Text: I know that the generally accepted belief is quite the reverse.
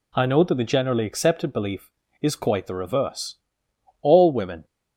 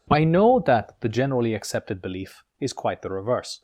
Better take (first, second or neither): second